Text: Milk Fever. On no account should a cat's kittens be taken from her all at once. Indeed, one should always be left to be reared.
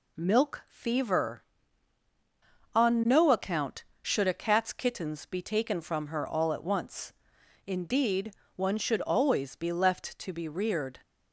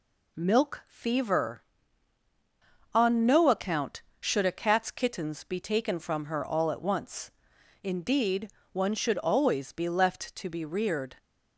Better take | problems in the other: neither | none

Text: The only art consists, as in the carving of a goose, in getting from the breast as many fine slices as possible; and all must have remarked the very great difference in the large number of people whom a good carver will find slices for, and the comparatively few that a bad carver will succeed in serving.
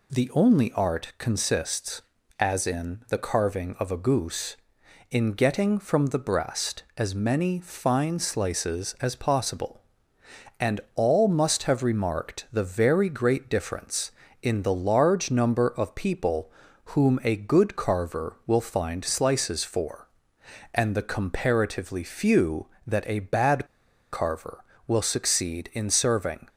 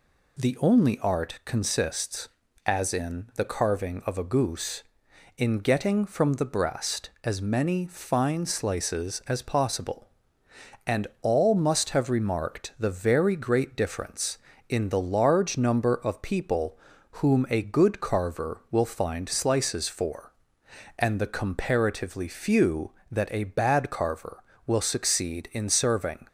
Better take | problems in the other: second | pauses between "and" and "all"; slight; at 10.8 s; 0.16 s long; slight in the second // pauses between "people" and "whom"; slight; at 16.5 s; 0.36 s long; slight in the second // pauses between "bad" and "carver"; noticeable; at 23.6 s; 0.47 s long

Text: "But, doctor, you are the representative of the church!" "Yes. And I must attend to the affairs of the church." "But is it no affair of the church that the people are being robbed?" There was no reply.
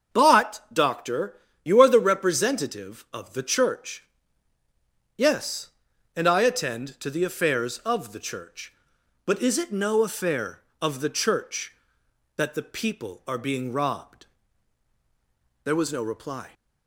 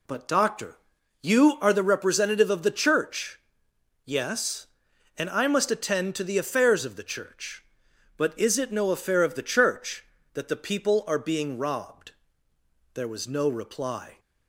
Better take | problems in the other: second | starts louder than the rest; until 1.2 s; 7 dB // skips "must"; at 6.4 s

